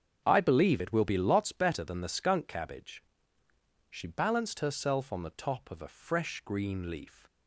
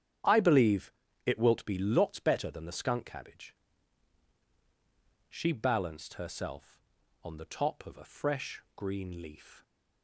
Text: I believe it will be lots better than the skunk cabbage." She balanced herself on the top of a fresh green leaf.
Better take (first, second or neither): first